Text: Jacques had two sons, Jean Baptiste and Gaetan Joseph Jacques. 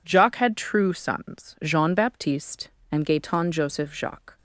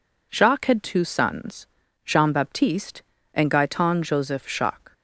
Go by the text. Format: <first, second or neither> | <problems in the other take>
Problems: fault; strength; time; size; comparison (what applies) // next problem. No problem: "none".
second | says "true" for "two"; at 0.5 s